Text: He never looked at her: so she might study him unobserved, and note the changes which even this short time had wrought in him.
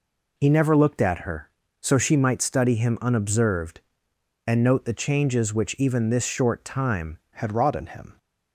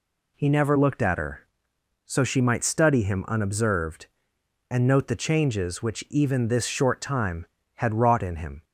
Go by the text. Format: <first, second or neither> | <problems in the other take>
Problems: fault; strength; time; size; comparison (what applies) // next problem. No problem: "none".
second | changes voice at "had"; from 7.3 s on; 0.8 s long